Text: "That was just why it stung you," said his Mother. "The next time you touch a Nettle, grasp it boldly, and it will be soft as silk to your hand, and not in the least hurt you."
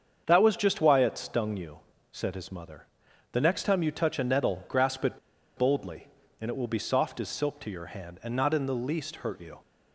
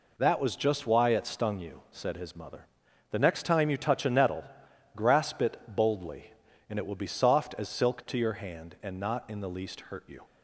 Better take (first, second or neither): second